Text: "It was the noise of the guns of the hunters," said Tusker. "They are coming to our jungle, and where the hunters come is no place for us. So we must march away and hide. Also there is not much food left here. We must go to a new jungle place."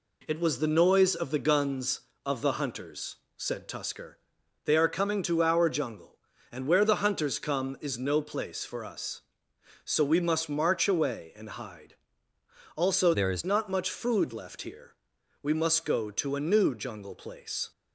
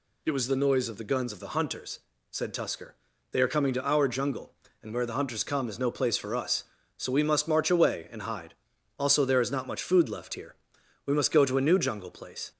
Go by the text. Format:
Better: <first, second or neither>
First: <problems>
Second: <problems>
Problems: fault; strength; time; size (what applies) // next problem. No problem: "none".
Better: second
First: changes voice from "there" to "is"; from 13.1 to 13.4 s; 0.3 s long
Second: none